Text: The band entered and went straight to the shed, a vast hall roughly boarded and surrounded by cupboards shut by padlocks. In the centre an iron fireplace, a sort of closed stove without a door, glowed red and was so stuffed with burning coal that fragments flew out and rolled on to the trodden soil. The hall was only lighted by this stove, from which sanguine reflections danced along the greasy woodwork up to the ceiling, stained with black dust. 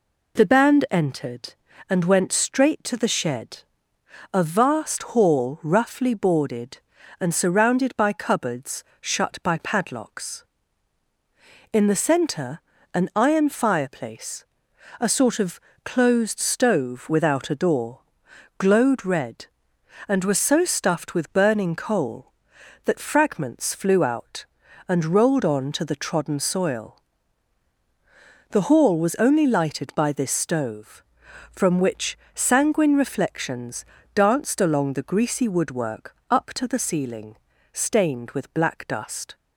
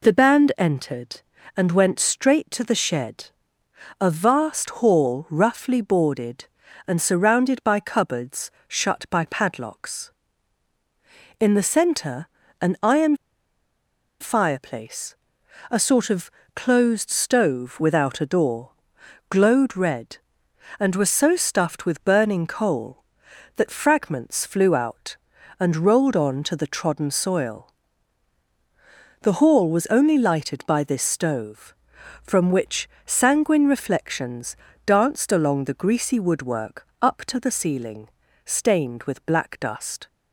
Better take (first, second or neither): first